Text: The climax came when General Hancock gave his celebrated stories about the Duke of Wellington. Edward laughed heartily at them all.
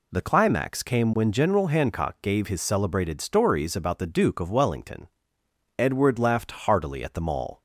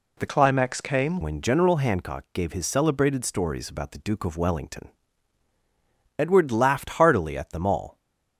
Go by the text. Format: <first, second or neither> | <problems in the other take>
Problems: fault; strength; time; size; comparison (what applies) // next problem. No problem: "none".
first | changes voice from "climax" to "came"; from 0.2 to 1.2 s; 1.0 s long